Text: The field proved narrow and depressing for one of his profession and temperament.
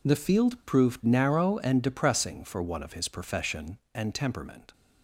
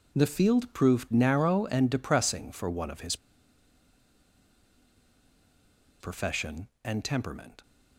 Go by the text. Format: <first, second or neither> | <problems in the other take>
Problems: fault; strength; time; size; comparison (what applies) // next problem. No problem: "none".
first | pauses between "his" and "profession"; strong; at 3.1 s; 2.8 s long